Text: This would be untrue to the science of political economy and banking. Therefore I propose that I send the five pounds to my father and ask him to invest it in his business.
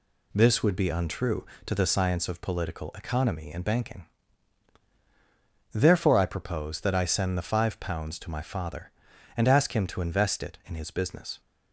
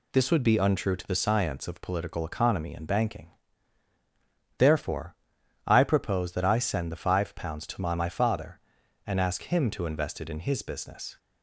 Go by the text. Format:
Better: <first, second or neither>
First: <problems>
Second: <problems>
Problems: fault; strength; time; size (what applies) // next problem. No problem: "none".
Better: first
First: none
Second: pauses between "Therefore" and "I"; noticeable; at 5.1 s; 0.52 s long // says "my" twice; at 7.9 s